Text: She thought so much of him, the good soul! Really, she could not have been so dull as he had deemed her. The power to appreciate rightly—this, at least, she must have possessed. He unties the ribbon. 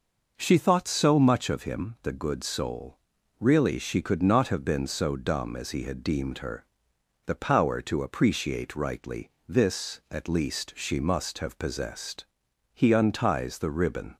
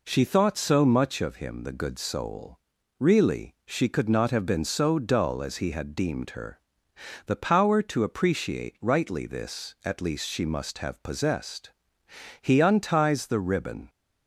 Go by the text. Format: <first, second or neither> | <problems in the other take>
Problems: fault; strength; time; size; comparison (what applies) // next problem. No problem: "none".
second | says "dumb" for "dull"; at 5.1 s